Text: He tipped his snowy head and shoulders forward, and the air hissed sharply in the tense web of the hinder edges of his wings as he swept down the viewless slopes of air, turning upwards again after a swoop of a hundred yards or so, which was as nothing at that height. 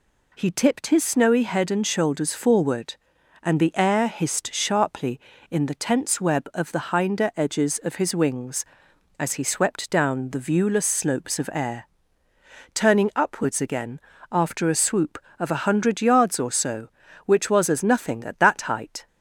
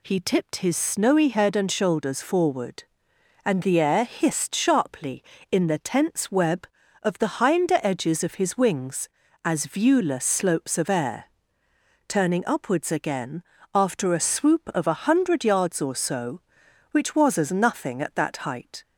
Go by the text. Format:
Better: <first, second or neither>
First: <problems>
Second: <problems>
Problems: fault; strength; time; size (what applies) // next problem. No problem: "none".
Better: first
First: pauses between "again" and "after"; slight; at 13.9 s; 0.32 s long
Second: skips "he swept down the"; at 9.6 s // pauses between "again" and "after"; slight; at 13.4 s; 0.28 s long